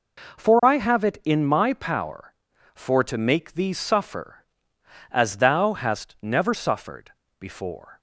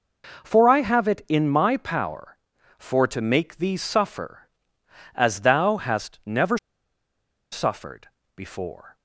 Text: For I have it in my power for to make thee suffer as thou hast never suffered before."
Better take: first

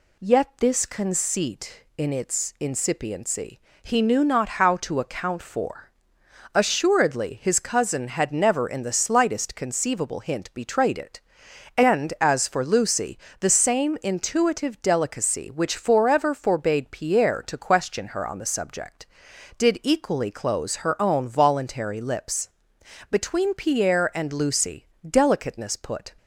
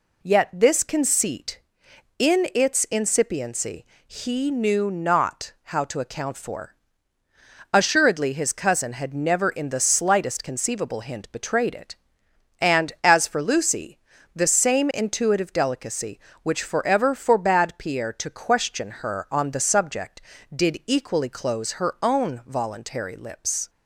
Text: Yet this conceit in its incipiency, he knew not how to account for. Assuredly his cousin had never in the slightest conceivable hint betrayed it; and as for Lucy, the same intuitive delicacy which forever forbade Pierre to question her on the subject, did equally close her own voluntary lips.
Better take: second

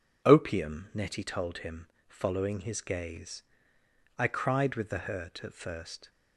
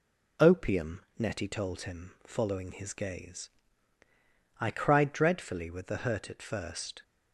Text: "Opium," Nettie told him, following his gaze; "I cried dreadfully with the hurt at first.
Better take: second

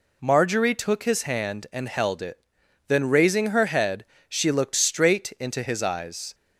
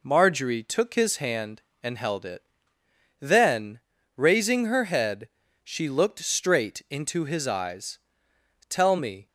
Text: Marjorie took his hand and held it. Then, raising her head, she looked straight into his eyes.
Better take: first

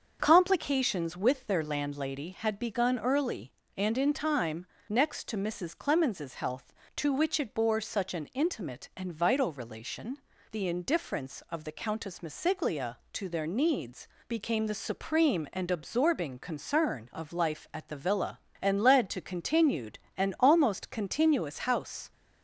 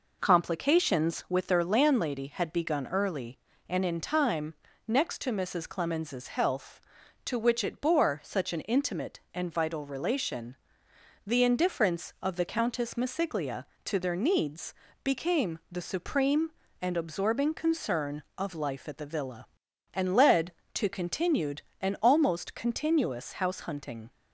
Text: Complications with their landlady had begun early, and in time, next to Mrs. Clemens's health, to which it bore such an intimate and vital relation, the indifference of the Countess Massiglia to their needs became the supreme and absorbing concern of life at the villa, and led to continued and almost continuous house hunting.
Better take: second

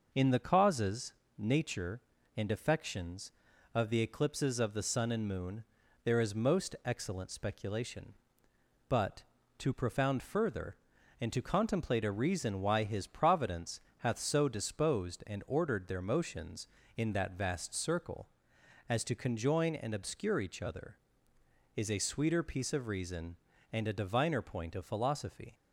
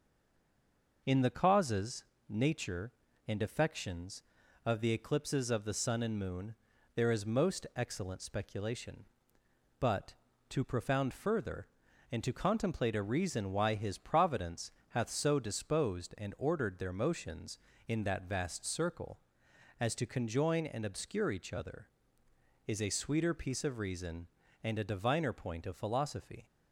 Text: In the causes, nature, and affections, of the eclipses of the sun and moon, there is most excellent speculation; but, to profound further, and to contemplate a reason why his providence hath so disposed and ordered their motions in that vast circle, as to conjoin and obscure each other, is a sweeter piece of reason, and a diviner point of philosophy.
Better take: first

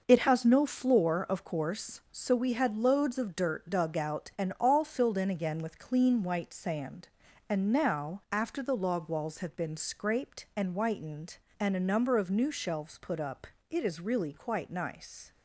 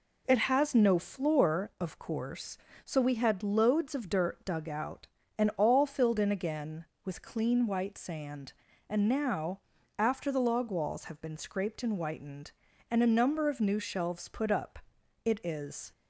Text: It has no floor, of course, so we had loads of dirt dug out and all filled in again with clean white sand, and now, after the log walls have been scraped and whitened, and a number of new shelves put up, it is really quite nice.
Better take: first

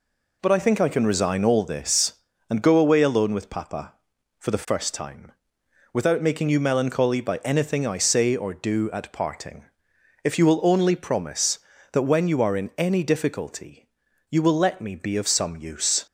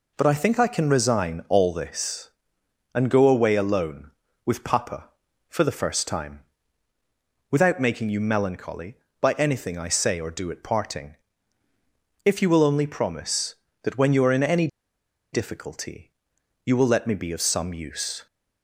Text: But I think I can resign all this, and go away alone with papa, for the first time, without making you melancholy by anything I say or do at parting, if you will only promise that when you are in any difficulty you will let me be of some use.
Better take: first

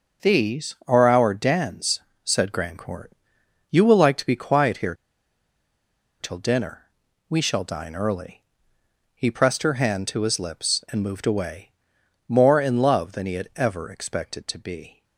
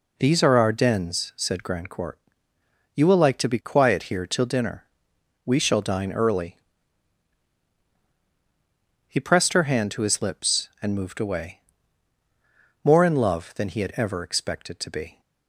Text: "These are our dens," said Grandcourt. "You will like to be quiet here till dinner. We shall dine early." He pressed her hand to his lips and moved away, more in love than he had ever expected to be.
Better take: second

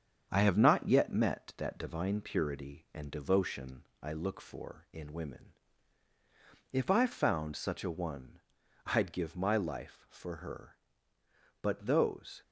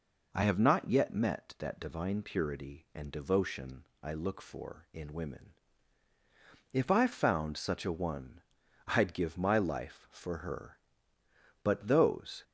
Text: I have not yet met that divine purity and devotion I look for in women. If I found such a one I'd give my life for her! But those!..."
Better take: second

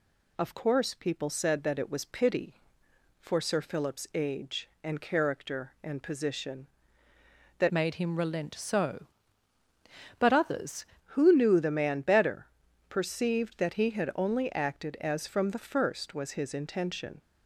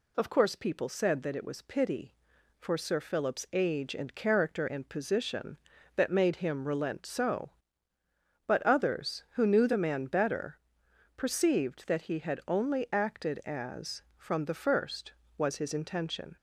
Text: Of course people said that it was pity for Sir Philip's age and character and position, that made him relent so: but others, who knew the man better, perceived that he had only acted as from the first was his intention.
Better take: second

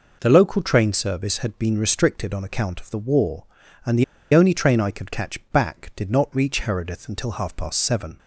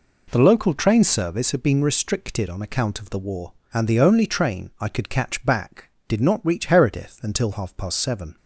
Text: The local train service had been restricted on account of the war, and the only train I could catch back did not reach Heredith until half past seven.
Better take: second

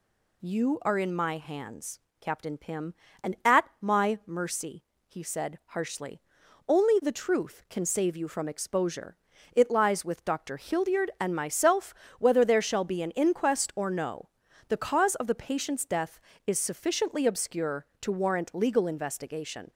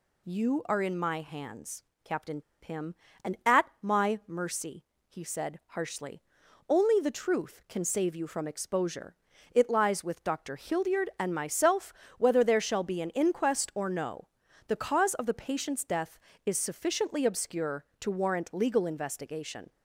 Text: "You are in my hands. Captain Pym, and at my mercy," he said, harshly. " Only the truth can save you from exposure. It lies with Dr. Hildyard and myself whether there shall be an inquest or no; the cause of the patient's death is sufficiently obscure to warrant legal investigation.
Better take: first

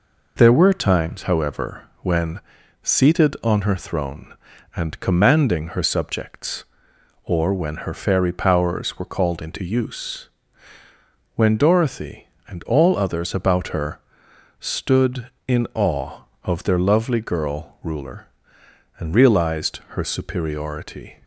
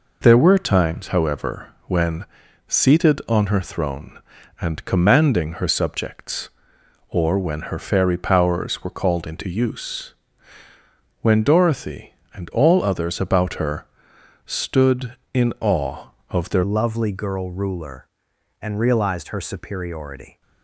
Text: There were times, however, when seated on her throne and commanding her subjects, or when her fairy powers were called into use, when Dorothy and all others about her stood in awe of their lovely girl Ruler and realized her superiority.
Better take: first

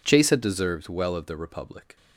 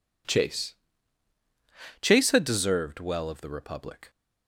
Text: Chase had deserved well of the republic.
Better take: first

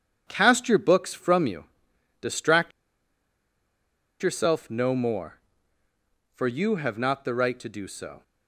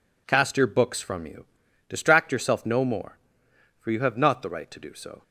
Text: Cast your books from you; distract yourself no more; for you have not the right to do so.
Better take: second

